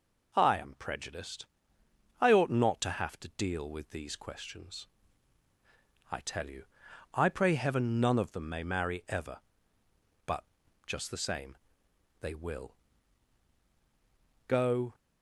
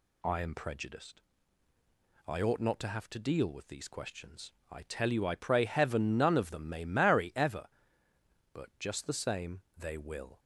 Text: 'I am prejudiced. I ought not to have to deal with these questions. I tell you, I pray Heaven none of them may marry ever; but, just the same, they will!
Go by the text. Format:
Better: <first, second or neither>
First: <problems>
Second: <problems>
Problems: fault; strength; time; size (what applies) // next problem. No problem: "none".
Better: second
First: goes on to say "Go"; slight; from 14.4 s on; 0.48 s long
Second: none